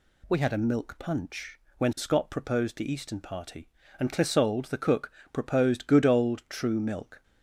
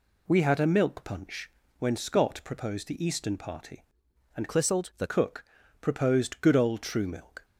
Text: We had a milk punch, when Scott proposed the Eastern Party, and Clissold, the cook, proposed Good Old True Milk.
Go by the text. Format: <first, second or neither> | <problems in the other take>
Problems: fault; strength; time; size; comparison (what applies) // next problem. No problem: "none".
first | changes voice from "Clissold" to "the"; from 4.4 to 5.0 s; 0.6 s long